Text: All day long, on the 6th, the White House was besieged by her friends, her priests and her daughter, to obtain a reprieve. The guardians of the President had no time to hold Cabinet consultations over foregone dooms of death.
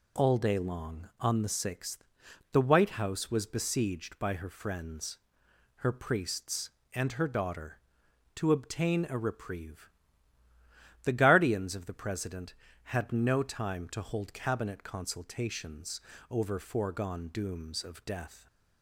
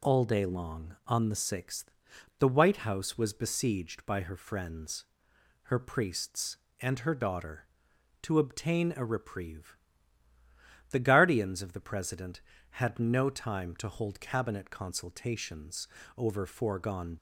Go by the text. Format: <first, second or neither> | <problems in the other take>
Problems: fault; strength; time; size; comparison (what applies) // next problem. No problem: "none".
first | pauses between "consultations" and "over"; slight; at 15.8 s; 0.30 s long; slight in the first // stops before "dooms of death"; at 17.1 s